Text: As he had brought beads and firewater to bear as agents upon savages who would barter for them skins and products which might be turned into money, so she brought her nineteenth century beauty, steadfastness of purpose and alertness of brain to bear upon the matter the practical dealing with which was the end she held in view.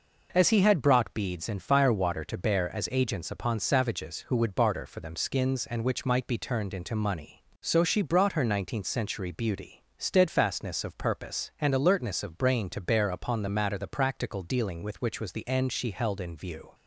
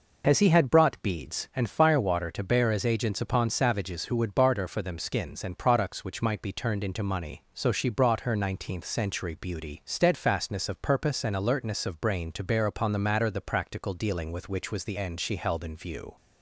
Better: second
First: skips "products"; at 5.8 s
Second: none

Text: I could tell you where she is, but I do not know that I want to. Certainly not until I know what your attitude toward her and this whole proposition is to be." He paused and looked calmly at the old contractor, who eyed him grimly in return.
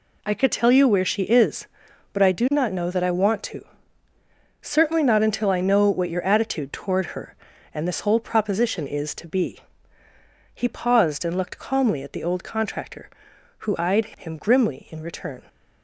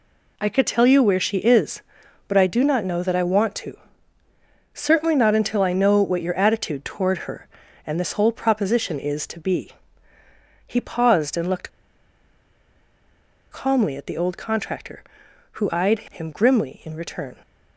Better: first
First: none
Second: pauses between "looked" and "calmly"; strong; at 11.6 s; 1.8 s long

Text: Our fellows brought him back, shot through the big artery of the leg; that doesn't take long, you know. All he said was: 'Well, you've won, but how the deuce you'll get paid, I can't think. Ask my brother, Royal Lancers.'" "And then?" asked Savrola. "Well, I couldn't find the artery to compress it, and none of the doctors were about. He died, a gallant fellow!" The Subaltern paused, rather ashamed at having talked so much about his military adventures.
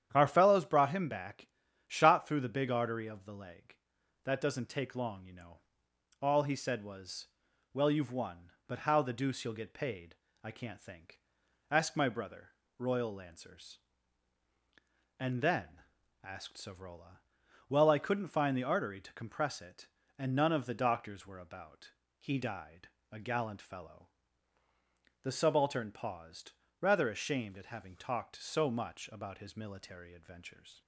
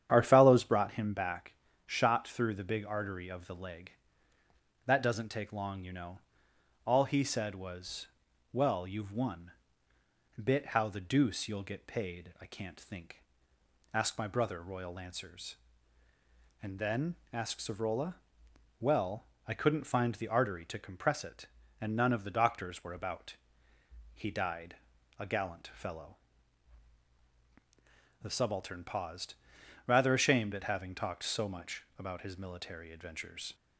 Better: first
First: starts louder than the rest; strong; until 1.1 s; 9.5 dB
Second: starts louder than the rest; strong; until 1.1 s; 9.5 dB // says "bit" for "but"; at 10.4 s // pauses between "much" and "about"; slight; at 31.8 s; 0.16 s long

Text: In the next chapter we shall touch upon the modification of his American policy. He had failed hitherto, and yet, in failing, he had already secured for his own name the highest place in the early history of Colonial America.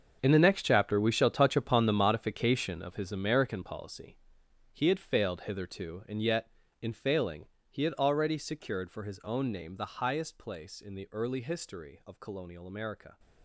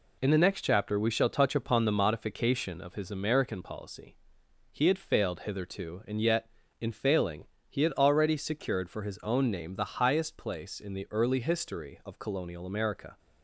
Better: second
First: gets quieter; strong; throughout; 14.5 dB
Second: none

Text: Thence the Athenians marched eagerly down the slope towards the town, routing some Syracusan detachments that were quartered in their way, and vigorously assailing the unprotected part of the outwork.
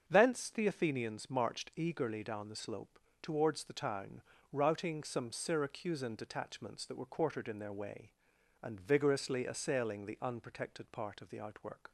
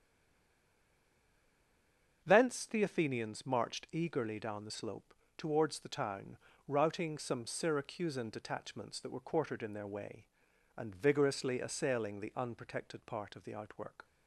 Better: first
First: starts louder than the rest; until 1.0 s; 7 dB // pauses between "slope" and "towards"; slight; at 3.0 s; 0.21 s long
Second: stays silent before the first word; until 2.2 s; 2.2 s long // starts louder than the rest; until 3.2 s; 6.5 dB // pauses between "slope" and "towards"; slight; at 5.1 s; 0.22 s long

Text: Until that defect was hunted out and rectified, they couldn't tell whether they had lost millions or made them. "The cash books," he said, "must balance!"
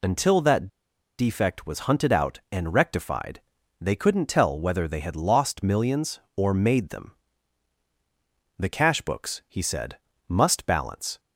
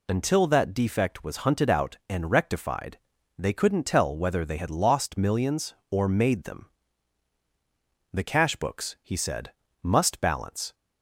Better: second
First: pauses between "that" and "defect"; noticeable; at 0.6 s; 0.51 s long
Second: none

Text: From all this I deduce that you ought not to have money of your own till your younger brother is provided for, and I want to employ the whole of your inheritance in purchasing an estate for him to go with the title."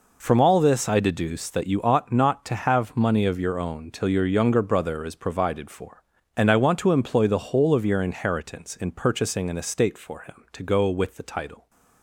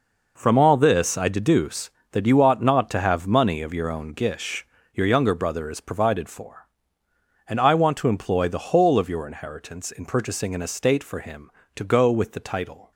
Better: first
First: none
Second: says "gish" for "till"; at 4.1 s

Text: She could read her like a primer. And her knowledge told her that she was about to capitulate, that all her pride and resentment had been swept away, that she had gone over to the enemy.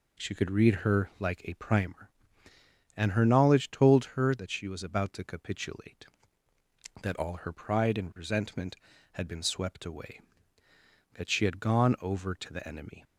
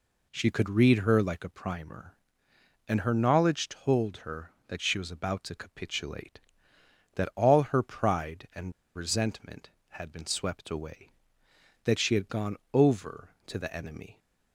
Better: first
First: none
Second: pauses between "and" and "resentment"; slight; at 8.7 s; 0.24 s long // pauses between "gone" and "over"; slight; at 12.5 s; 0.16 s long

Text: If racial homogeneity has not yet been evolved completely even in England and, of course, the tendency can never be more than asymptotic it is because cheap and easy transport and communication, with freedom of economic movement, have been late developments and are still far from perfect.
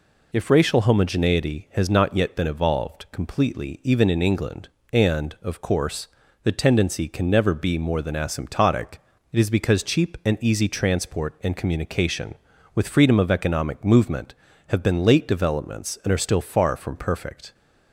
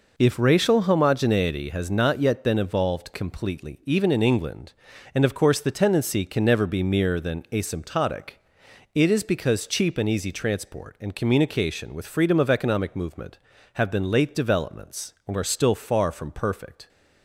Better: first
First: pauses between "asymptotic" and "it"; slight; at 8.9 s; 0.34 s long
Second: says "mere" for "more"; at 6.8 s // pauses between "asymptotic" and "it"; noticeable; at 8.3 s; 0.64 s long

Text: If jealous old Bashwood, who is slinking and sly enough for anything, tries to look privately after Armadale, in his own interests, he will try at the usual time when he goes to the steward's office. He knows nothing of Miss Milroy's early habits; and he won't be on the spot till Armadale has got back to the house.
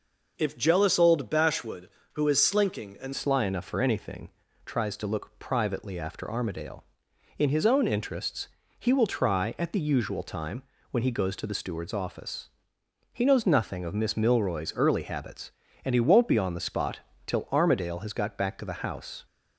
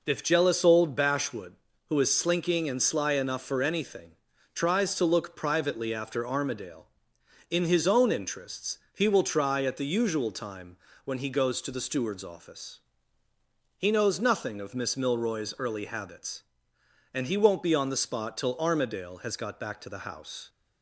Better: second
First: changes voice at "sly"; from 3.1 s on; 16.1 s long // pauses between "time" and "when"; slight; at 10.6 s; 0.28 s long // pauses between "spot" and "till"; slight; at 16.9 s; 0.26 s long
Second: pauses between "time" and "when"; slight; at 10.7 s; 0.28 s long

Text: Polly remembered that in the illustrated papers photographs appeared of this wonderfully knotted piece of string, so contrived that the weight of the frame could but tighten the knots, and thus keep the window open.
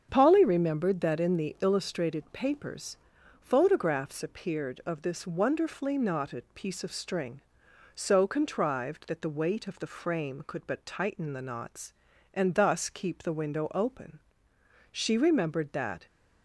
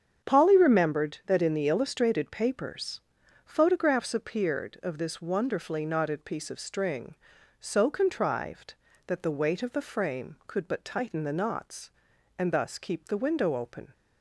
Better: second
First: starts louder than the rest; strong; until 1.1 s; 7 dB // pauses between "papers" and "photographs"; at 2.9 s; 0.42 s long // goes on to say "She remembered that"; noticeable; from 14.9 s on; 1.1 s long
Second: starts louder than the rest; strong; until 1.3 s; 7.5 dB // pauses between "papers" and "photographs"; at 3.0 s; 0.44 s long

